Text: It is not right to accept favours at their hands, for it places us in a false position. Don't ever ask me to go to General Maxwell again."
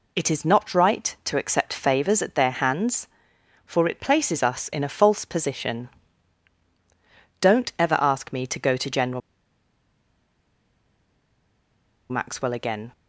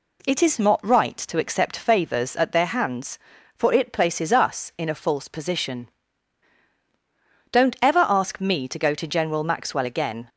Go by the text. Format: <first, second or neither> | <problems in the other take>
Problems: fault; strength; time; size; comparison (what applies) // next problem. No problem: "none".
second | pauses between "General" and "Maxwell"; strong; at 9.2 s; 2.8 s long